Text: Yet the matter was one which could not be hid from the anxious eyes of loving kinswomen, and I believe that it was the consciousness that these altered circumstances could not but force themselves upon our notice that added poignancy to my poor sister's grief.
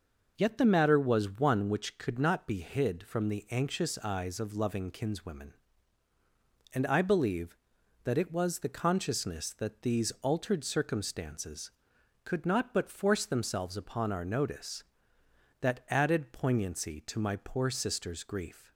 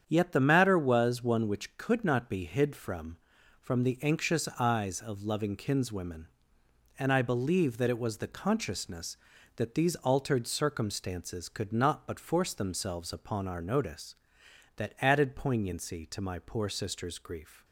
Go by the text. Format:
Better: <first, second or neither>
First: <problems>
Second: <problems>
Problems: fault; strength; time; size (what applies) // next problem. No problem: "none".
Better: first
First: none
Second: starts louder than the rest; strong; until 1.0 s; 8 dB // says "from" twice; at 3.6 s